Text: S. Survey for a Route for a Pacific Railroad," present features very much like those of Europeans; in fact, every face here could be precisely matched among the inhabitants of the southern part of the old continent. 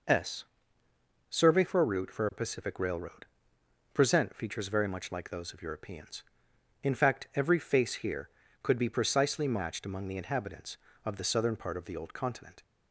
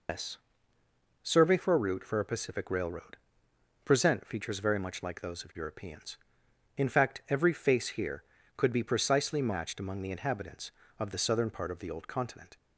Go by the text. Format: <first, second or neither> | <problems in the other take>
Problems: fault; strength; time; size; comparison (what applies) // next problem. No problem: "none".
first | loses the start of "S"; at 0.0 s; 90 ms